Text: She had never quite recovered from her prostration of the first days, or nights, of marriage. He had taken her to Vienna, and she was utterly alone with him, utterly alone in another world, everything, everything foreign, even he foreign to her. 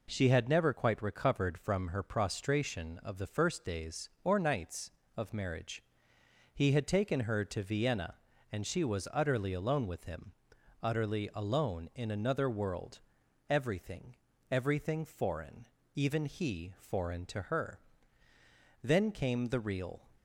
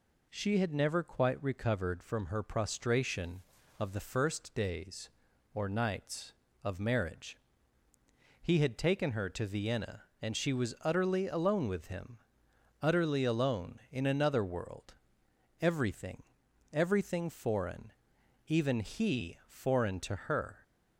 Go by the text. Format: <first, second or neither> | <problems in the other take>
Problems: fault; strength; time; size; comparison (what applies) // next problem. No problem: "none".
second | goes on to say "Then came the real"; noticeable; from 18.8 s on; 1.2 s long